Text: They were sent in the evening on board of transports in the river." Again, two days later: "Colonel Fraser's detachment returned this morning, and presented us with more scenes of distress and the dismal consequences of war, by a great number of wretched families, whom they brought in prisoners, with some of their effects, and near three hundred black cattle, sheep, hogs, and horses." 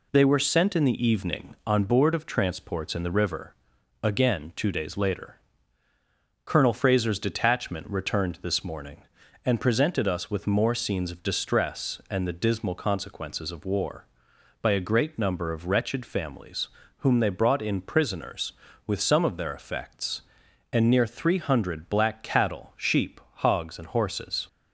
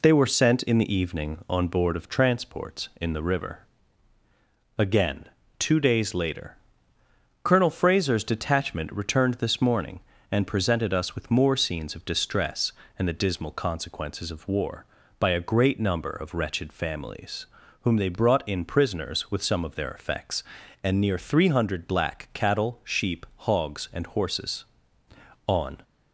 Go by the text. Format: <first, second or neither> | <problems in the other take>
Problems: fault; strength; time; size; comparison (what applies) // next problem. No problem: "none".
first | goes on to say "On"; slight; from 25.4 s on; 0.36 s long